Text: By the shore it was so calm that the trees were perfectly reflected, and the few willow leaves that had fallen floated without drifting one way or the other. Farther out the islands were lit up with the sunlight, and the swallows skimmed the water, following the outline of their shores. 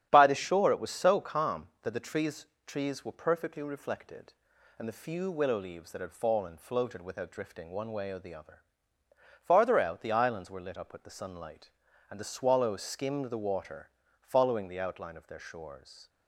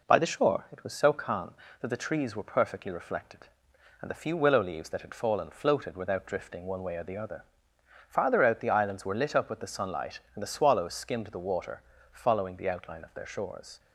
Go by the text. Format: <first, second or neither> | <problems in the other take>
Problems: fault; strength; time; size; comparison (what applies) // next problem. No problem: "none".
second | starts louder than the rest; strong; until 1.1 s; 10 dB // says "trees" twice; at 2.6 s